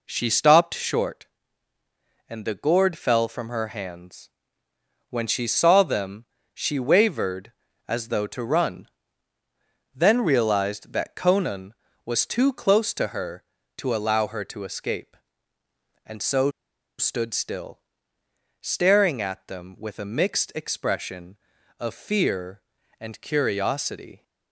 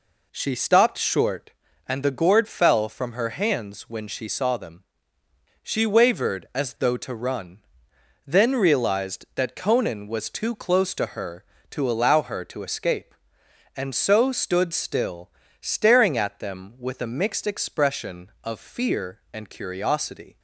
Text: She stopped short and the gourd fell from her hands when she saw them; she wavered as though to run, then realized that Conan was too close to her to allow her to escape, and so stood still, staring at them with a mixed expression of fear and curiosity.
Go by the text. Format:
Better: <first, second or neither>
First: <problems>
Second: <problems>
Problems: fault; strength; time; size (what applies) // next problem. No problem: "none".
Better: second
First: pauses between "hands" and "when"; noticeable; at 4.2 s; 0.80 s long // pauses between "so" and "stood"; noticeable; at 16.4 s; 0.48 s long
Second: none